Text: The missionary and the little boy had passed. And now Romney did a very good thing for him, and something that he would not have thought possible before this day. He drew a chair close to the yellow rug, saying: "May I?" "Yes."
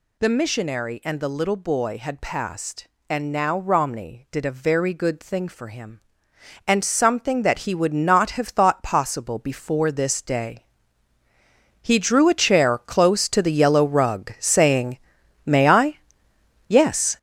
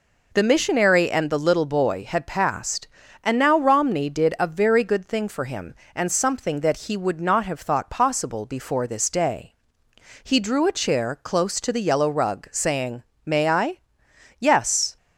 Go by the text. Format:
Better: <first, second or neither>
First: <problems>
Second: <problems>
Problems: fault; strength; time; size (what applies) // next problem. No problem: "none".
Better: second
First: gets louder; strong; throughout; 8.5 dB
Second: none